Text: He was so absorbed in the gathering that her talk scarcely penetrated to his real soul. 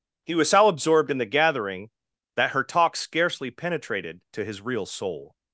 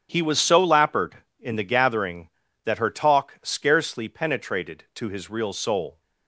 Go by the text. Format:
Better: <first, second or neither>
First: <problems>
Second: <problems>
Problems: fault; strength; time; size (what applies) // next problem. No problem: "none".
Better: first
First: none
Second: starts louder than the rest; strong; until 1.1 s; 10 dB // says "lappered" for "absorbed"; at 0.6 s